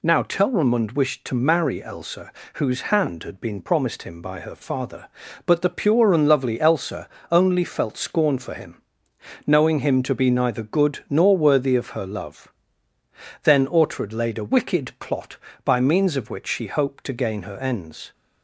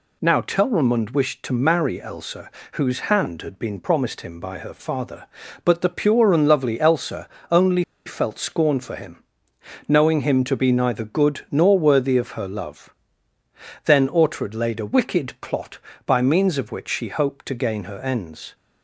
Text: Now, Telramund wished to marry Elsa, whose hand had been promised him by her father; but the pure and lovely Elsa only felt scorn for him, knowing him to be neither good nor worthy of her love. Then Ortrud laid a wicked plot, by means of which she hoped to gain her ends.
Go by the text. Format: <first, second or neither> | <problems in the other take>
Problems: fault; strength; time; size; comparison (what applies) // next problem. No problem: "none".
first | pauses between "Elsa" and "only"; slight; at 7.2 s; 0.22 s long; slight in the first // pauses between "only" and "felt"; slight; at 7.8 s; 0.23 s long